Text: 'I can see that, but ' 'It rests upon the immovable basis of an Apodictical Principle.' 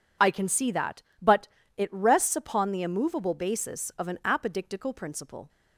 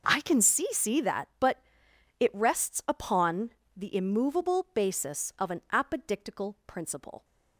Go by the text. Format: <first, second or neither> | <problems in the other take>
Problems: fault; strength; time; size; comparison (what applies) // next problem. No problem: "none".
first | says "see" twice; at 0.7 s // pauses between "upon" and "the"; slight; at 3.5 s; 0.22 s long